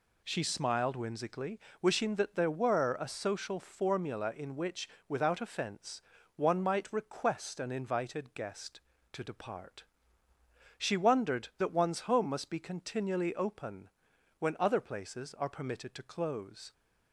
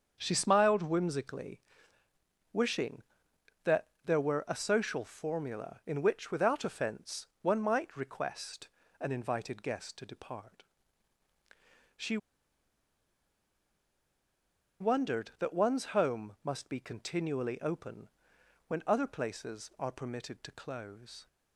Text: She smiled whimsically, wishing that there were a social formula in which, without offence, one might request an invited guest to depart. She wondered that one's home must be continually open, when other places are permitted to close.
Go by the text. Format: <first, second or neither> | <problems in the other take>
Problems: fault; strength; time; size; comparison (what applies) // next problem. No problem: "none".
first | starts louder than the rest; strong; until 1.1 s; 7 dB // pauses between "that" and "there"; slight; at 3.8 s; 0.16 s long // pauses between "request" and "an"; slight; at 8.6 s; 0.32 s long // pauses between "She" and "wondered"; strong; at 12.1 s; 2.6 s long